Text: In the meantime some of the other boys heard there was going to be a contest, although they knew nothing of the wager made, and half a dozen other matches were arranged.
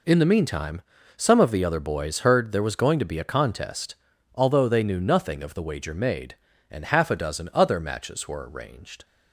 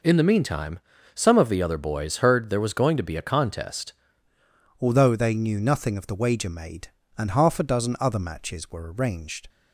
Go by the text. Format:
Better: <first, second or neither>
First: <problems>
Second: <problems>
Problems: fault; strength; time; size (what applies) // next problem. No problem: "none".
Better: first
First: pauses between "meantime" and "some"; slight; at 0.8 s; 0.34 s long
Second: pauses between "meantime" and "some"; slight; at 0.7 s; 0.34 s long // changes voice at "although"; from 4.8 s on; 4.6 s long